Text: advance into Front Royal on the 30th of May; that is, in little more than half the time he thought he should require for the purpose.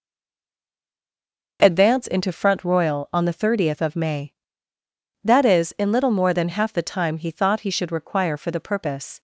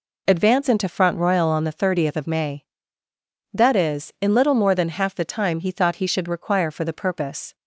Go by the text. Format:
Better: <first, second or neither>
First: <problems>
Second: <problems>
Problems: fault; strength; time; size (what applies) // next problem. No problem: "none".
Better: second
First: stays silent before the first word; noticeable; until 1.5 s; 1.5 s long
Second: none